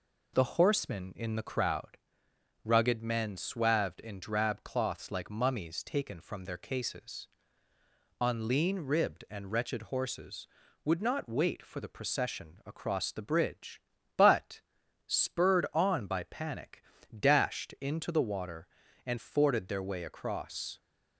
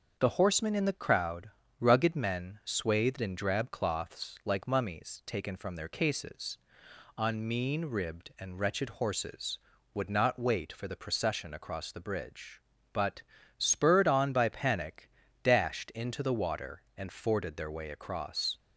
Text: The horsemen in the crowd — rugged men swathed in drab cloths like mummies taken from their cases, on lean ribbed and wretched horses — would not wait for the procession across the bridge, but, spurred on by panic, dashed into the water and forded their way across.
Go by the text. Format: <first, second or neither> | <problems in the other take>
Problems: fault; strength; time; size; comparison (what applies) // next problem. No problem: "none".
first | starts louder than the rest; until 1.2 s; 6.5 dB // says "mean" for "lean"; at 7.4 s